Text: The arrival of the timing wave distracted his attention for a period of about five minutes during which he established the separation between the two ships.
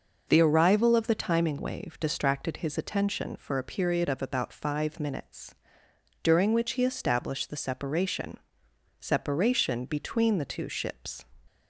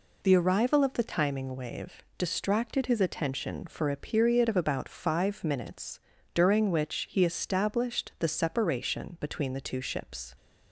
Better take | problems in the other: second | pauses between "minutes" and "during"; noticeable; at 5.5 s; 0.68 s long; slight in the second // says "separation" twice; at 9.0 s

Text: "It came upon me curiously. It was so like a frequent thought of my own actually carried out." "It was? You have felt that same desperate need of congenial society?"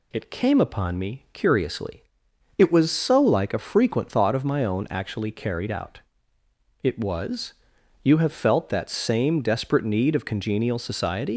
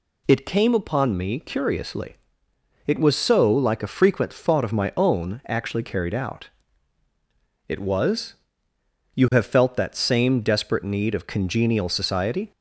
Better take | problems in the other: second | leaves "society" unfinished; at 11.3 s; 125 ms

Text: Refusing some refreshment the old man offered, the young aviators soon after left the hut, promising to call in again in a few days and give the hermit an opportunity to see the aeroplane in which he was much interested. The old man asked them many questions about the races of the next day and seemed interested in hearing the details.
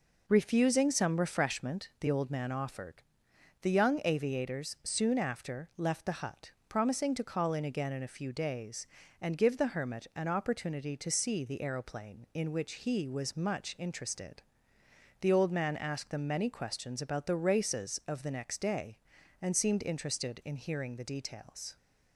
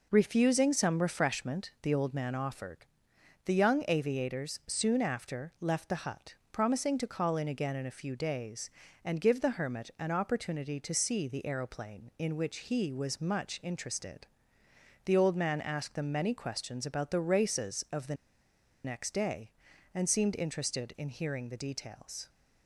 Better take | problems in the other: first | pauses between "the" and "next"; noticeable; at 18.1 s; 0.70 s long

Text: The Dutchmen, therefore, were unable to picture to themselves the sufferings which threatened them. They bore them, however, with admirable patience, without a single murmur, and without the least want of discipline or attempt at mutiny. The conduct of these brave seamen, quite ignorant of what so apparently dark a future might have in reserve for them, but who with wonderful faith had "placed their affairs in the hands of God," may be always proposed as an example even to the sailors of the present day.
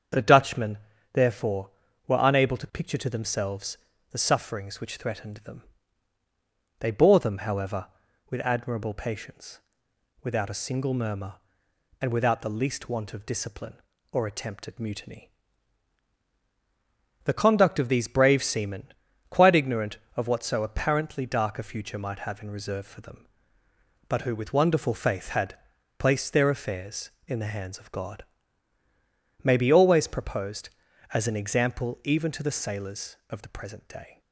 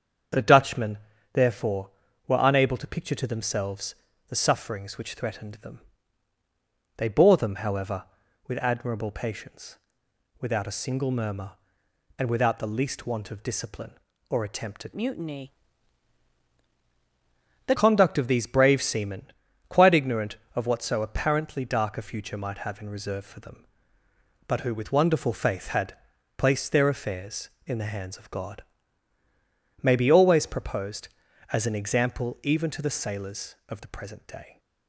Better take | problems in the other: first | starts louder than the rest; strong; until 1.7 s; 7.5 dB; strong in the first // pauses between "themselves" and "the"; slight; at 3.9 s; 0.36 s long; slight in the first // changes voice from "mutiny" to "The"; from 14.9 to 17.7 s; 2.8 s long // pauses between "had" and "placed"; at 25.9 s; 0.40 s long; also in the first

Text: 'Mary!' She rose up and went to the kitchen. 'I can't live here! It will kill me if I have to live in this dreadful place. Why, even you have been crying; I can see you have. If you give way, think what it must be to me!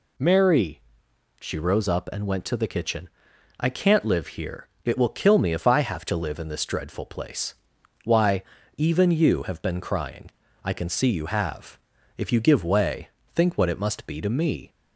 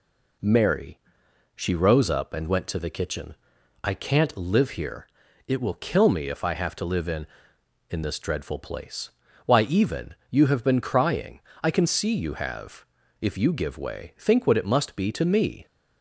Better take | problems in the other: first | says "in" twice; at 7.8 s // pauses between "even" and "you"; slight; at 10.1 s; 0.16 s long

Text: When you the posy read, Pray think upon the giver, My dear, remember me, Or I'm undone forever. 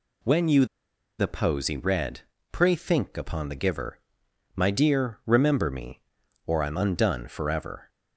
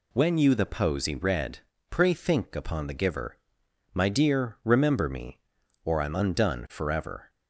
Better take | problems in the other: second | pauses between "you" and "the"; noticeable; at 0.6 s; 0.53 s long

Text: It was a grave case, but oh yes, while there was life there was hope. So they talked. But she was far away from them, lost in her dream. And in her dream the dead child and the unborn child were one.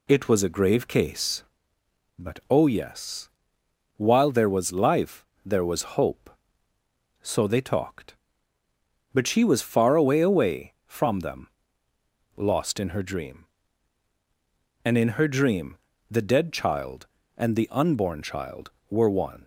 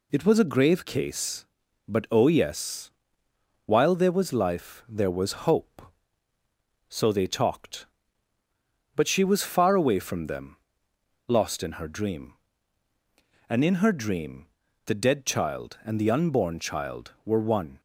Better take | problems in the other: second | pauses between "life" and "there"; slight; at 5.2 s; 0.22 s long // says "away" twice; at 10.1 s // pauses between "dream" and "the"; slight; at 15.7 s; 0.34 s long; also in the second

